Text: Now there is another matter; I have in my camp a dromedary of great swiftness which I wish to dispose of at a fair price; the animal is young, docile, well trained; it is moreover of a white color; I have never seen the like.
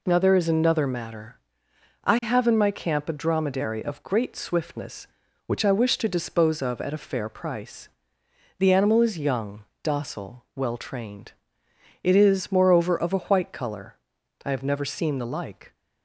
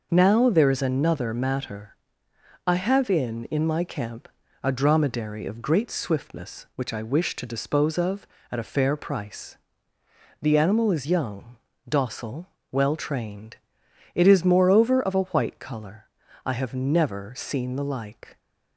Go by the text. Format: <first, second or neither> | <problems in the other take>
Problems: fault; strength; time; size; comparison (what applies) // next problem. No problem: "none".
first | says "in" twice; at 3.4 s // pauses between "camp" and "a"; slight; at 4.2 s; 0.34 s long